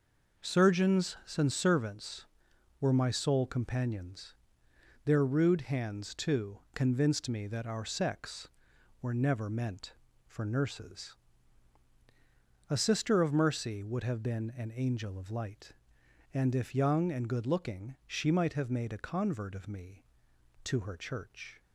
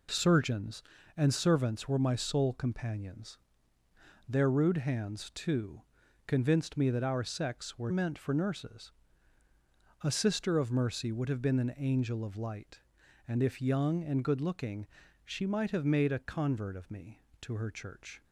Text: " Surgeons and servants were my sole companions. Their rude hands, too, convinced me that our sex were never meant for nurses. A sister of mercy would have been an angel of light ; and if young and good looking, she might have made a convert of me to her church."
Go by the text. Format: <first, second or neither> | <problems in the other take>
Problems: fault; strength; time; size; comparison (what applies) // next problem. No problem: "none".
first | skips "never"; at 7.9 s